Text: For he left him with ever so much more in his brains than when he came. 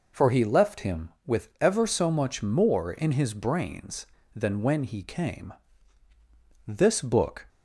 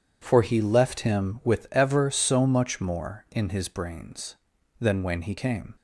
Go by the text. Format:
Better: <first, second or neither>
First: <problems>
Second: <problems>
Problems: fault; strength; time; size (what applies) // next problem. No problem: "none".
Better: second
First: goes on to say "This book"; noticeable; from 6.6 s on; 0.80 s long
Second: none